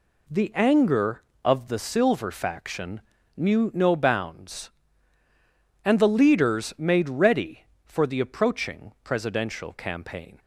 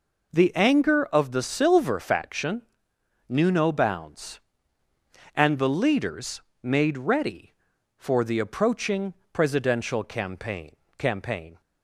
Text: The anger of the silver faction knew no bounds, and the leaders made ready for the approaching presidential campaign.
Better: first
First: pauses between "faction" and "knew"; slight; at 3.0 s; 0.36 s long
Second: pauses between "faction" and "knew"; noticeable; at 2.6 s; 0.66 s long // pauses between "leaders" and "made"; slight; at 6.4 s; 0.22 s long // pauses between "approaching" and "presidential"; slight; at 9.1 s; 0.18 s long // says "campaign" twice; at 10.9 s

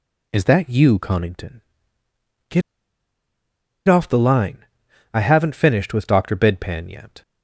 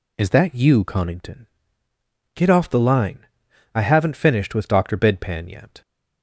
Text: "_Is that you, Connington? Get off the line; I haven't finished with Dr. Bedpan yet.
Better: second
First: pauses between "Get" and "off"; strong; at 2.6 s; 1.2 s long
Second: none

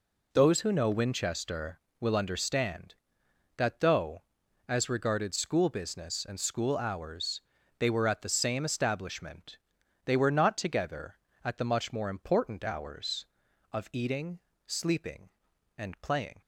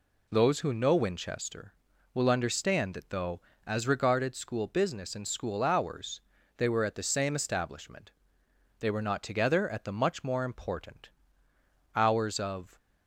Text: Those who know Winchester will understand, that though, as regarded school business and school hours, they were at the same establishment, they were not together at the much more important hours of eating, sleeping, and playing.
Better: first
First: none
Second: pauses between "important" and "hours"; noticeable; at 11.0 s; 0.86 s long // stops before "eating sleeping and playing"; at 12.7 s

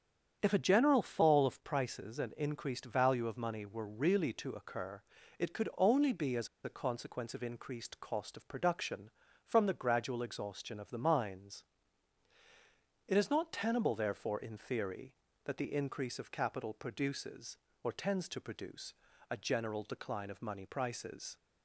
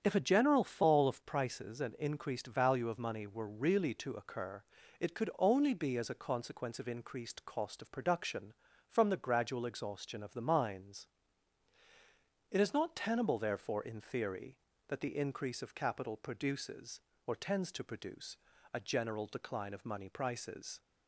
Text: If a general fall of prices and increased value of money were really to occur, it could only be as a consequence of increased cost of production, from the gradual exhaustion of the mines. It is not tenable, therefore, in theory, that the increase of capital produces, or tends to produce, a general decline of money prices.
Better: second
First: starts louder than the rest; strong; until 1.4 s; 8 dB // pauses between "as" and "a"; slight; at 6.4 s; 0.16 s long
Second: starts louder than the rest; strong; until 1.0 s; 8 dB

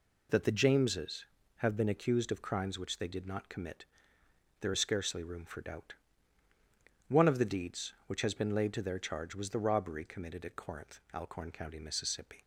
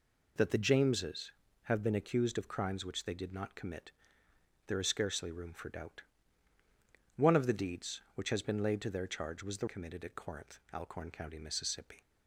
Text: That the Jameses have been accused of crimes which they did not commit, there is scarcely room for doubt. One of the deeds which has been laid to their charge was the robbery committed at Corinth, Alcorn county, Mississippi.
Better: first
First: none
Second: skips "robbery"; at 9.6 s

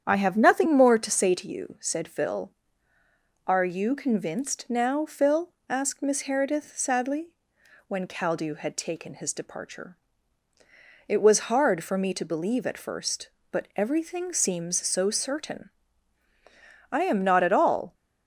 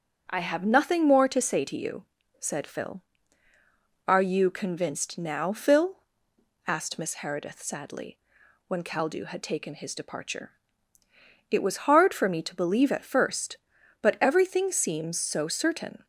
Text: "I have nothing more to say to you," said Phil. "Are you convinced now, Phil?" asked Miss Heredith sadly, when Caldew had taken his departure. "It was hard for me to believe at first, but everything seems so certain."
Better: second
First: starts louder than the rest; strong; until 1.0 s; 8.5 dB // goes on to say "I am not at all"; noticeable; from 16.9 s on; 1.0 s long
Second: starts louder than the rest; strong; until 1.2 s; 7.5 dB

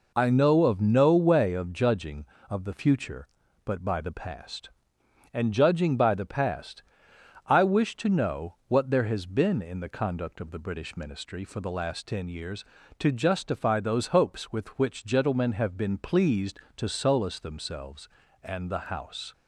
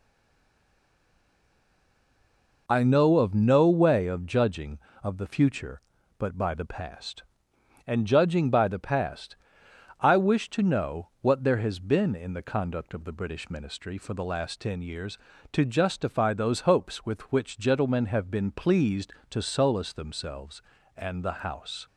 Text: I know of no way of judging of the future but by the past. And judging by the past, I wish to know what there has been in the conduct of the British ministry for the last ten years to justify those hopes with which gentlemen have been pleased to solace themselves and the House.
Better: first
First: none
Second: stays silent before the first word; strong; until 2.6 s; 2.6 s long

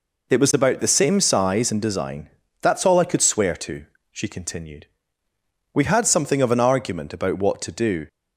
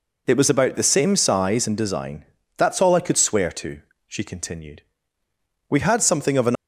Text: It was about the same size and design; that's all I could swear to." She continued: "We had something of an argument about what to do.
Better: first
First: none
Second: stops before "argument about what to do"; at 6.5 s

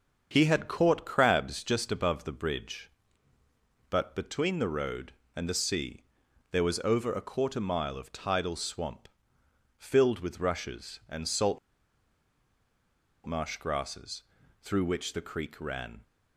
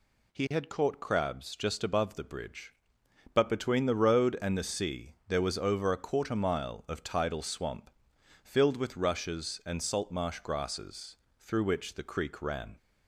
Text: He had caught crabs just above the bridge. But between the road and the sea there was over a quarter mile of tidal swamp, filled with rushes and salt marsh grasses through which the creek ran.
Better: second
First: starts louder than the rest; until 1.3 s; 7 dB // pauses between "sea" and "there"; noticeable; at 6.0 s; 0.48 s long // pauses between "salt" and "marsh"; strong; at 11.5 s; 1.6 s long // pauses between "grasses" and "through"; at 14.2 s; 0.40 s long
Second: pauses between "grasses" and "through"; slight; at 11.1 s; 0.22 s long

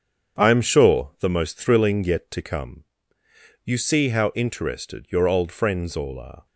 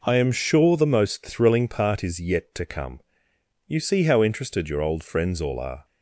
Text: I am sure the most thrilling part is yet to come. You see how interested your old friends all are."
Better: second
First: starts louder than the rest; strong; until 1.4 s; 8 dB // skips "part is"; at 2.0 s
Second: none

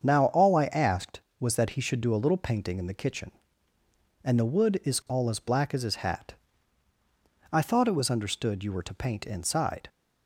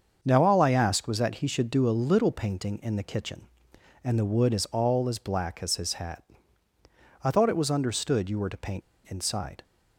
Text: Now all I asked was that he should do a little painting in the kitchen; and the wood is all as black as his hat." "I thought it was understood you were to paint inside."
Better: first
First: starts louder than the rest; strong; until 1.0 s; 7 dB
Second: starts louder than the rest; until 1.2 s; 7 dB // pauses between "paint" and "inside"; slight; at 8.8 s; 0.25 s long

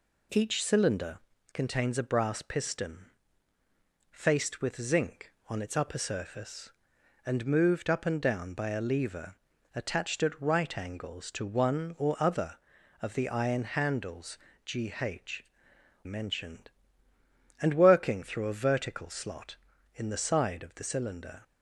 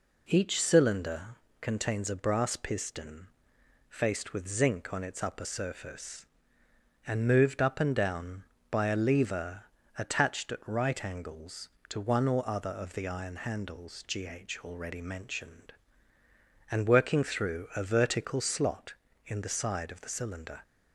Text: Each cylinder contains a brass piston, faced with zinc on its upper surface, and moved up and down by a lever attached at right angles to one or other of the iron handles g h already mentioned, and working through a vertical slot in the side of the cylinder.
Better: second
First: pauses between "cylinder" and "contains"; slight; at 1.1 s; 0.36 s long // pauses between "lever" and "attached"; at 9.3 s; 0.40 s long // pauses between "handles" and "g"; slight; at 14.3 s; 0.28 s long // skips "already"; at 15.7 s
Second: pauses between "cylinder" and "contains"; slight; at 1.3 s; 0.26 s long // pauses between "lever" and "attached"; slight; at 9.6 s; 0.34 s long

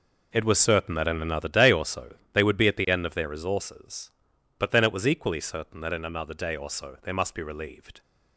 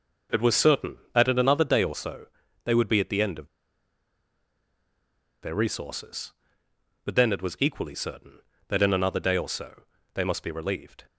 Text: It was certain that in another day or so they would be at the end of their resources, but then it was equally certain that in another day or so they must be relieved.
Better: first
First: pauses between "so" and "they"; slight; at 2.1 s; 0.18 s long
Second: pauses between "so" and "they"; slight; at 2.2 s; 0.36 s long // pauses between "of" and "their"; strong; at 3.4 s; 1.9 s long // pauses between "so" and "they"; slight; at 9.8 s; 0.34 s long

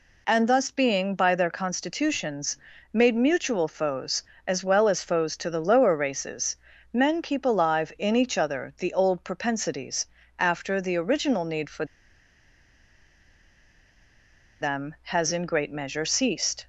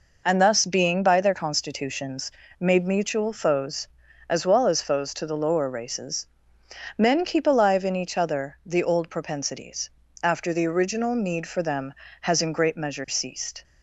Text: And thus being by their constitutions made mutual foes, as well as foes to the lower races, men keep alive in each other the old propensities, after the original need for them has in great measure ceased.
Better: second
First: pauses between "constitutions" and "made"; at 2.5 s; 0.38 s long // pauses between "for" and "them"; strong; at 11.8 s; 2.7 s long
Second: pauses between "constitutions" and "made"; slight; at 2.3 s; 0.26 s long

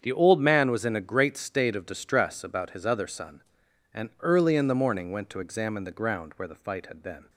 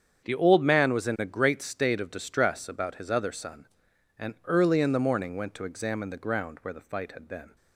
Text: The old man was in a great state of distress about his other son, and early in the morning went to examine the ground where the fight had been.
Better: neither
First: starts louder than the rest; strong; until 1.0 s; 7.5 dB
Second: starts louder than the rest; strong; until 1.2 s; 7.5 dB

